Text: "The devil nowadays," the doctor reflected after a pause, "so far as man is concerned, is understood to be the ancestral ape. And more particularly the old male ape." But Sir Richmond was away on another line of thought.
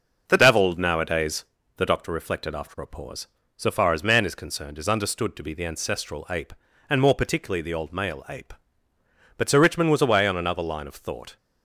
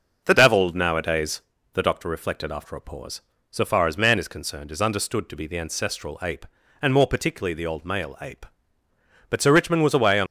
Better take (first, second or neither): first